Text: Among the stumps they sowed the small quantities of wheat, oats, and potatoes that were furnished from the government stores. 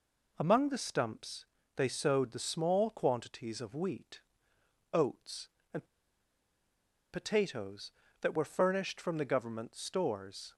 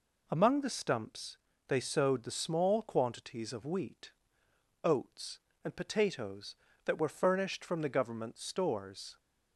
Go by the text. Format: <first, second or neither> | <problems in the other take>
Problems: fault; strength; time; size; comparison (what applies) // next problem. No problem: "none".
second | pauses between "stumps" and "they"; slight; at 1.4 s; 0.32 s long; slight in the second // pauses between "and" and "potatoes"; strong; at 5.8 s; 1.2 s long